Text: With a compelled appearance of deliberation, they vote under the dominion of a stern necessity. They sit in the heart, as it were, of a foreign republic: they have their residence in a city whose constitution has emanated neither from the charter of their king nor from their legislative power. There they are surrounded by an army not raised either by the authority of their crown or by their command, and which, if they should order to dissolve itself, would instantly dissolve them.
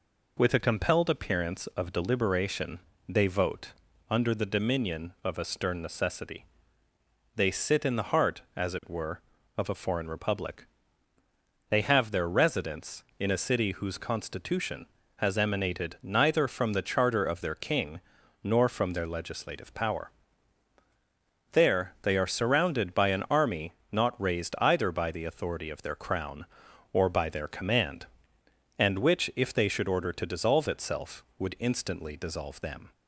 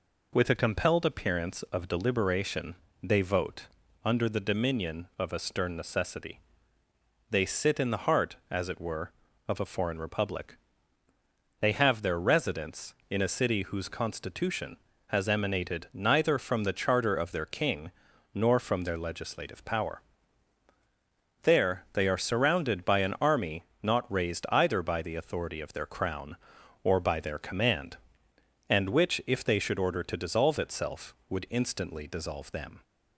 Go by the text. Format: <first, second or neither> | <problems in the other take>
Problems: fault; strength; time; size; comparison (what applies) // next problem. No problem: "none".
neither | pauses between "vote" and "under"; slight; the same in both // pauses between "king" and "nor"; the same in both // pauses between "army" and "not"; slight; the same in both